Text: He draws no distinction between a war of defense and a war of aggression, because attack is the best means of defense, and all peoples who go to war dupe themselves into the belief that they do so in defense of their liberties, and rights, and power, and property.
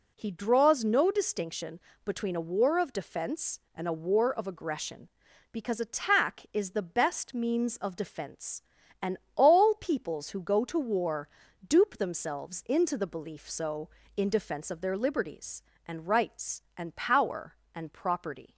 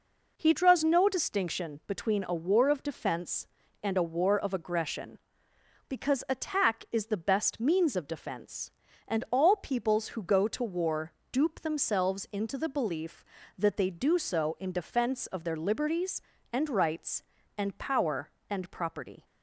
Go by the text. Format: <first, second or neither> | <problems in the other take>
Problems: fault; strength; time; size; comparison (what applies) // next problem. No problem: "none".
second | pauses between "distinction" and "between"; slight; at 1.7 s; 0.24 s long // pauses between "and" and "all"; slight; at 9.1 s; 0.18 s long // pauses between "war" and "dupe"; at 11.2 s; 0.38 s long; slight in the second // skips "that they do"; at 13.4 s